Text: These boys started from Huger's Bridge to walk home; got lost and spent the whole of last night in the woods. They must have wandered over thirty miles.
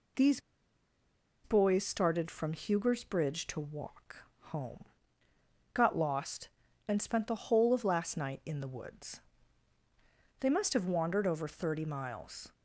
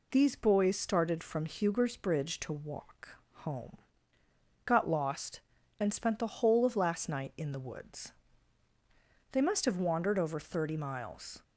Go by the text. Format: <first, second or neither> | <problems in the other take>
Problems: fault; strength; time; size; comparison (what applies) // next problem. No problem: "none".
second | pauses between "These" and "boys"; at 0.4 s; 1.0 s long // pauses between "walk" and "home"; slight; at 4.2 s; 0.22 s long; slight in the second